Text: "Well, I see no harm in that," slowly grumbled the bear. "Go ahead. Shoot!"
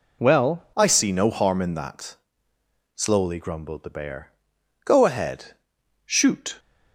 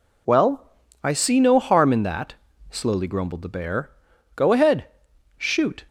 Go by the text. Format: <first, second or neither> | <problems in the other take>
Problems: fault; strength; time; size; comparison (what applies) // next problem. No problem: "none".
second | changes voice at "I"; from 0.7 s on; 5.8 s long